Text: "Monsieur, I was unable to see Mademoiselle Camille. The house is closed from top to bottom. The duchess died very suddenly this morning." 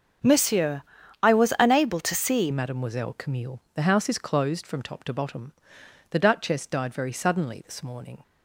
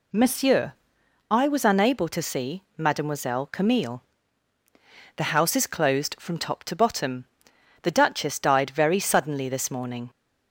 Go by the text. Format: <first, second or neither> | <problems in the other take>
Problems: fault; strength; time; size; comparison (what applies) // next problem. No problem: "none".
second | starts louder than the rest; until 1.6 s; 7 dB // changes voice at "Mademoiselle"; from 2.5 s on; 5.7 s long